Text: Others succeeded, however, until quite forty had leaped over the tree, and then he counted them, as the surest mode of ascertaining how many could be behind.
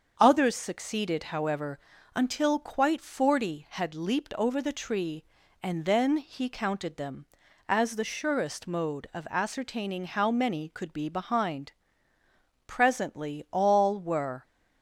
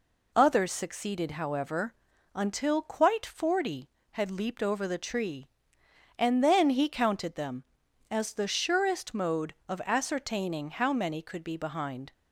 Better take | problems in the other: second | starts louder than the rest; until 1.2 s; 6.5 dB // goes on to say "Presently all were"; strong; from 12.6 s on; 1.7 s long

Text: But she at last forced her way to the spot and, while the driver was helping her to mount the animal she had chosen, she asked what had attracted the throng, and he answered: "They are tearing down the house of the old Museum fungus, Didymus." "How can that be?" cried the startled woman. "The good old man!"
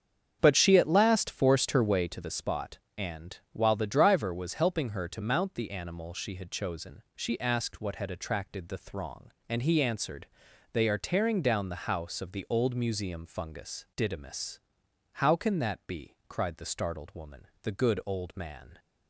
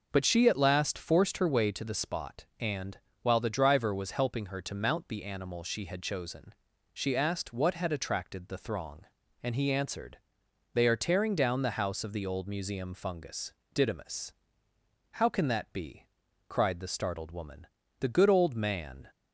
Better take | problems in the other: second | starts louder than the rest; strong; until 2.2 s; 7.5 dB

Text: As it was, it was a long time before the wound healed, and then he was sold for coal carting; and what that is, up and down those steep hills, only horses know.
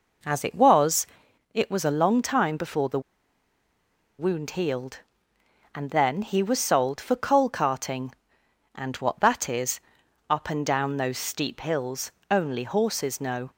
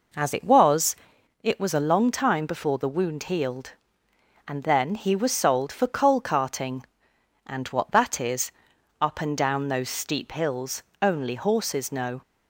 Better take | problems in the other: second | pauses between "the" and "wound"; at 2.9 s; 1.1 s long

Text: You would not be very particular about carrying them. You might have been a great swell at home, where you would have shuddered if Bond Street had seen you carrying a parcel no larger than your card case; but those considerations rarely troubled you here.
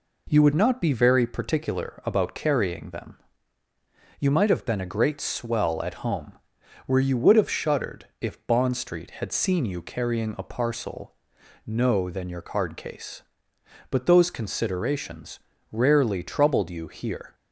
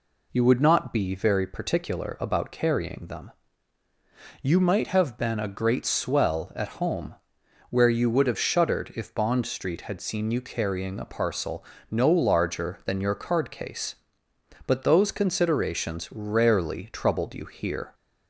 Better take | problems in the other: second | pauses between "parcel" and "no"; noticeable; at 11.1 s; 0.52 s long; slight in the second // skips "larger"; at 12.1 s // pauses between "considerations" and "rarely"; slight; at 15.3 s; 0.34 s long

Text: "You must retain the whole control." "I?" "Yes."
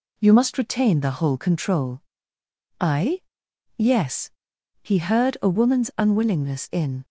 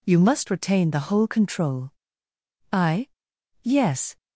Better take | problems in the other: second | goes on to say "He heard a woman's unwillingness in"; strong; from 4.8 s on; 2.2 s long

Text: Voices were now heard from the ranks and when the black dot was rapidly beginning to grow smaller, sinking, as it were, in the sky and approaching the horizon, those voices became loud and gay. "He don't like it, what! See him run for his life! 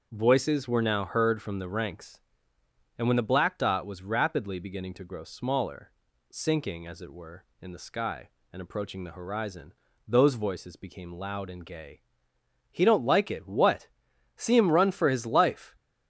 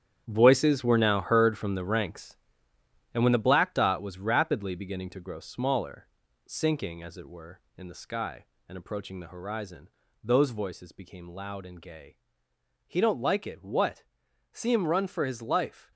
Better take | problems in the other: first | gets quieter; strong; throughout; 10 dB // starts louder than the rest; strong; until 1.2 s; 9.5 dB; also in the first

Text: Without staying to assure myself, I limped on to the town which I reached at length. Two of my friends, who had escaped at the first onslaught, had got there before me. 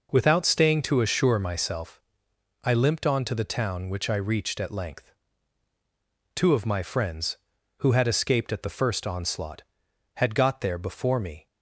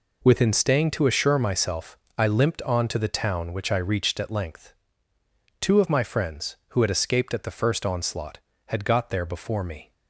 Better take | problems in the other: first | says "Within" for "Without"; at 0.2 s

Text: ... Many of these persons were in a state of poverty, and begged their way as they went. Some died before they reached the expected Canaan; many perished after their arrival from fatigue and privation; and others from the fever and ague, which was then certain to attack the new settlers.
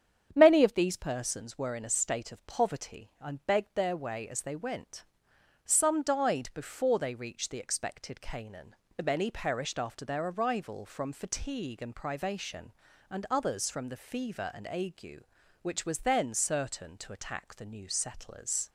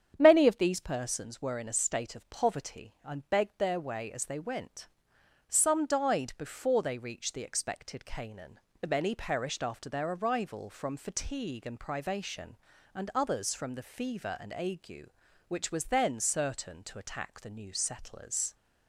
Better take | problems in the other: neither | starts louder than the rest; strong; the same in both

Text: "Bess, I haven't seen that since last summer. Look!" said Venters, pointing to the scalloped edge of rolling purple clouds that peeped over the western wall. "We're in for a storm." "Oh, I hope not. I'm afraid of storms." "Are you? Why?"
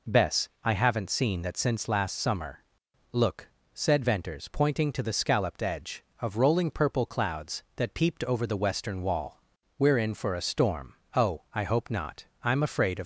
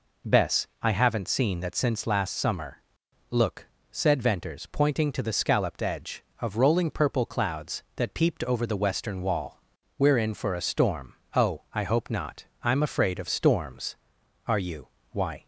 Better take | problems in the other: second | stops before "storms Are you Why"; at 13.0 s

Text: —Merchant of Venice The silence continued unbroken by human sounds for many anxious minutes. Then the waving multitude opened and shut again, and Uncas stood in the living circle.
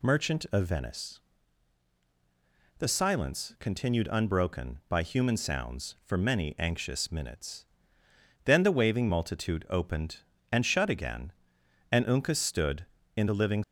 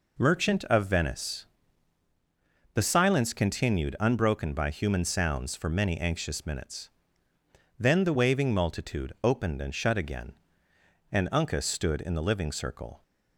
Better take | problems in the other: second | pauses between "Venice" and "The"; strong; at 1.1 s; 1.6 s long; strong in the second // stops before "circle"; at 13.6 s

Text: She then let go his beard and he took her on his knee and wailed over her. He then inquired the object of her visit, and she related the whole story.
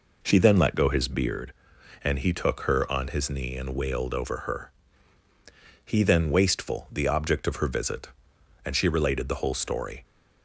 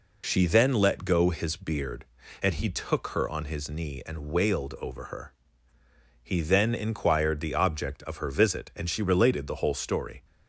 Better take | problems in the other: second | says "wasteful" for "inquired"; at 6.3 s

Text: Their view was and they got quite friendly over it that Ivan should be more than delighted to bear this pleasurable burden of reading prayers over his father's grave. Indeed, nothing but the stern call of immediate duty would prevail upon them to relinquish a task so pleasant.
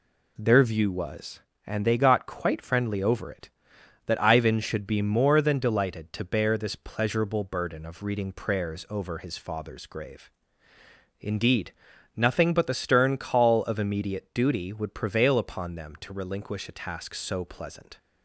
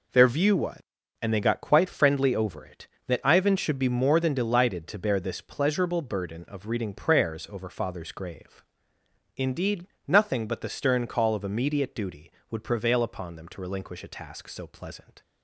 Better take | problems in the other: first | skips "his"; at 7.6 s

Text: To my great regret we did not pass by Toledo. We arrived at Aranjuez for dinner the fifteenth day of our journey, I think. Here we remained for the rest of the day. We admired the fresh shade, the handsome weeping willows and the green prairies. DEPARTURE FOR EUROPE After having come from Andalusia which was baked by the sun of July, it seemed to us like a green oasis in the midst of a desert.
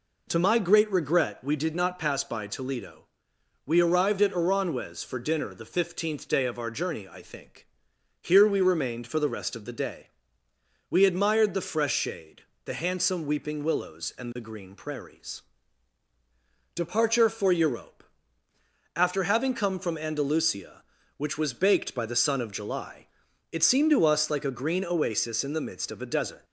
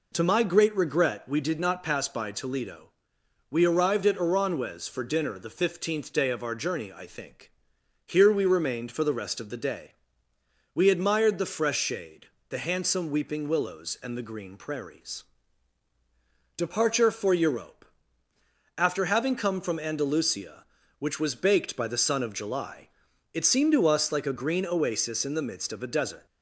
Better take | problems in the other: neither | pauses between "EUROPE" and "After"; noticeable; the same in both

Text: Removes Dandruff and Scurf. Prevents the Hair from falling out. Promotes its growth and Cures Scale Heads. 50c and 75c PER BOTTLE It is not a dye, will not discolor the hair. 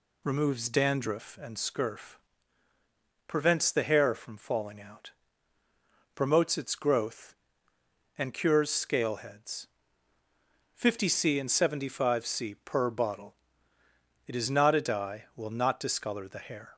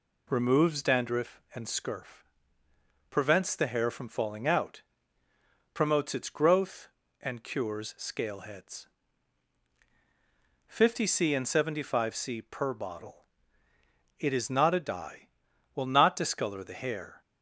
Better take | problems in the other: neither | pauses between "BOTTLE" and "It"; noticeable; the same in both

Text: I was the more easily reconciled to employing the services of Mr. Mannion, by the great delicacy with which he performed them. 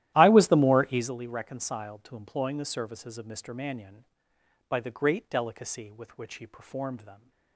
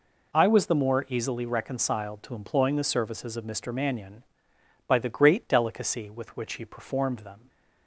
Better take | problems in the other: second | starts louder than the rest; strong; until 1.1 s; 14 dB

